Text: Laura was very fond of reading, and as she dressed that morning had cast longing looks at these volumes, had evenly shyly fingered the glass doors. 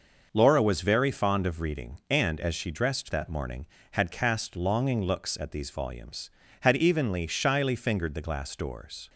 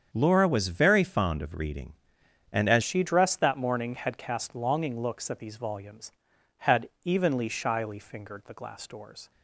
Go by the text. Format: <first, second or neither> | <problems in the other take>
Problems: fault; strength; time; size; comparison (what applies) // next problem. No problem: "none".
first | starts louder than the rest; strong; until 1.1 s; 7.5 dB // changes voice at "she"; from 2.8 s on; 6.5 s long // pauses between "had" and "evenly"; slight; at 6.8 s; 0.16 s long